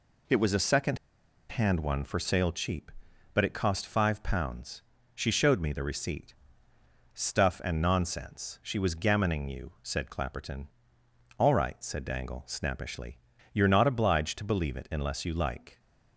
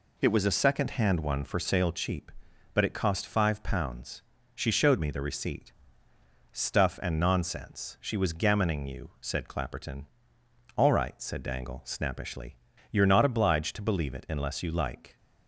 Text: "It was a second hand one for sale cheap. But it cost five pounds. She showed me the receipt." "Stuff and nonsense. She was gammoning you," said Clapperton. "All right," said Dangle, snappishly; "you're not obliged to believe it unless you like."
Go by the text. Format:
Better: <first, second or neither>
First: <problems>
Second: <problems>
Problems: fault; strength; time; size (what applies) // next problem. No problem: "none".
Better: second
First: pauses between "second" and "hand"; noticeable; at 0.9 s; 0.53 s long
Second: none